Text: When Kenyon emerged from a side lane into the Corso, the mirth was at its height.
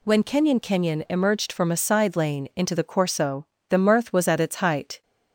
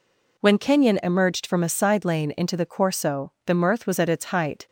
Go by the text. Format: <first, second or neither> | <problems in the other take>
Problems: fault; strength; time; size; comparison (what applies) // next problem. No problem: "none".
second | says "Kenyon" twice; at 0.5 s